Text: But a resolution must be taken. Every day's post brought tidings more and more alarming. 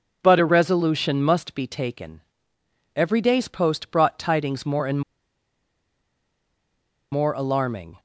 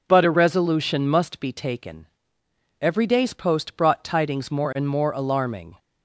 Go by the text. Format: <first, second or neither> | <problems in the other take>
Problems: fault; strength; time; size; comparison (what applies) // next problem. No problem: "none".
second | pauses between "and" and "more"; strong; at 5.0 s; 2.1 s long